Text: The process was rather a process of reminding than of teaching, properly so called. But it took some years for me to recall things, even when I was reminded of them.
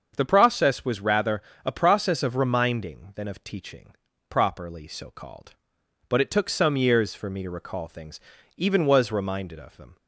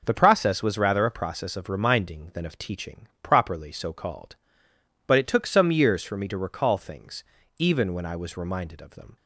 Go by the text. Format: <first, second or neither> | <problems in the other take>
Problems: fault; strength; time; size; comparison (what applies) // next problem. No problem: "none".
second | starts louder than the rest; until 1.1 s; 7 dB // pauses between "rather" and "a"; slight; at 1.4 s; 0.22 s long // skips "when I"; at 8.8 s